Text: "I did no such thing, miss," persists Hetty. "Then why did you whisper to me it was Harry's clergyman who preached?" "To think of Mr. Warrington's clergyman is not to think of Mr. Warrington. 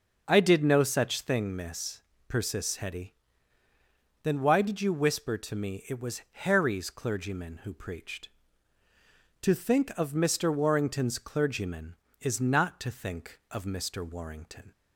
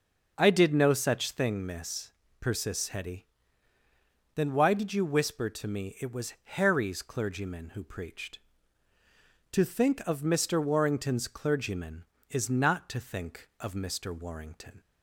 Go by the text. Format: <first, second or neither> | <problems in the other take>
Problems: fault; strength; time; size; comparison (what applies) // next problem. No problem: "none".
neither | starts louder than the rest; noticeable; the same in both